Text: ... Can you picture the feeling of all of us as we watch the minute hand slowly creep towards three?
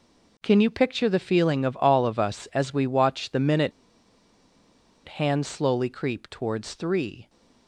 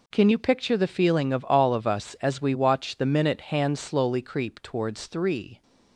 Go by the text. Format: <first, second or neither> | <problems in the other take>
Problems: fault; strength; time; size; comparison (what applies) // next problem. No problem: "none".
second | pauses between "minute" and "hand"; strong; at 3.7 s; 1.3 s long